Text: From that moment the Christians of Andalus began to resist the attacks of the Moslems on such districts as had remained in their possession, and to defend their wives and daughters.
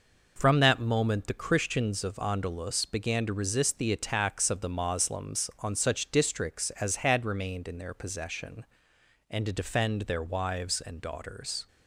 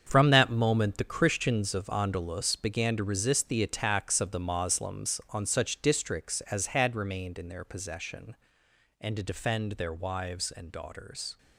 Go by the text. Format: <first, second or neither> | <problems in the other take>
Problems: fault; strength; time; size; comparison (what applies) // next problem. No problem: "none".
first | gets quieter; strong; throughout; 10.5 dB